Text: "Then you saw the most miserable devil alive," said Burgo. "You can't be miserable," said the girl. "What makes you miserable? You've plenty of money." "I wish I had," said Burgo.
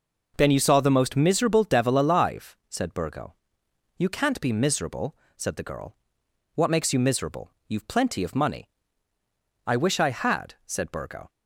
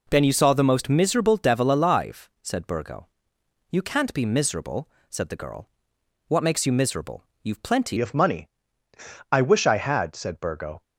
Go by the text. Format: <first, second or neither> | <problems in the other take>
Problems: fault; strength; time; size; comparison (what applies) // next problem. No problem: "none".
first | changes voice at "of"; from 7.9 s on; 2.9 s long